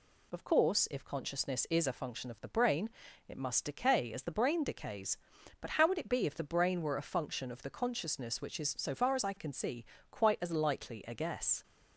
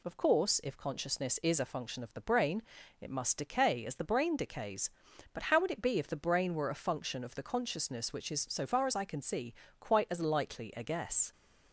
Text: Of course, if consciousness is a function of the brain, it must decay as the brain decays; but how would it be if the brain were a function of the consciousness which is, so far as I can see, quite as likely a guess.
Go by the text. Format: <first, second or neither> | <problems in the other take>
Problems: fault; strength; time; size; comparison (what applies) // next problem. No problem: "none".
neither | none